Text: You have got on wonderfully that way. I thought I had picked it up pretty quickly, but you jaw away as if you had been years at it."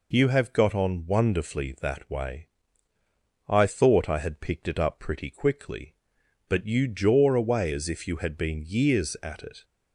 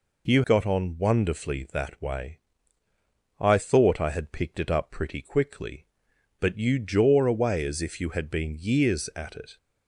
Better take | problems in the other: first | skips "have"; at 0.4 s

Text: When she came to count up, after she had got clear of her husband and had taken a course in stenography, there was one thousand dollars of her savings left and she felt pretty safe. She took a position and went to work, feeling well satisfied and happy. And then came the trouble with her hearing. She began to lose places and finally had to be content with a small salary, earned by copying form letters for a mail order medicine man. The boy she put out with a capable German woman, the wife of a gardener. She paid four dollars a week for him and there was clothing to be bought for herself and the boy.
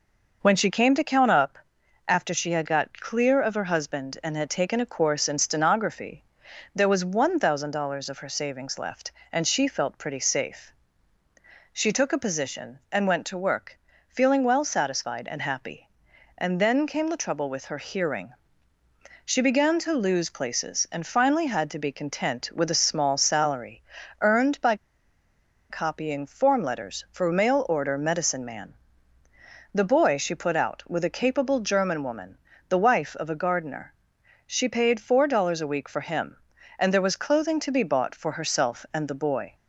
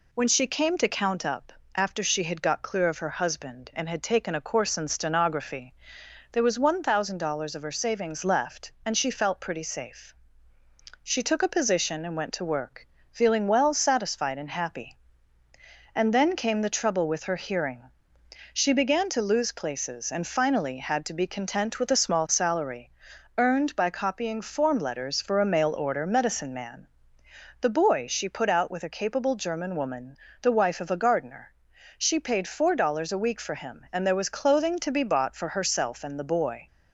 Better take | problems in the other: second | pauses between "by" and "copying"; noticeable; at 24.7 s; 0.95 s long

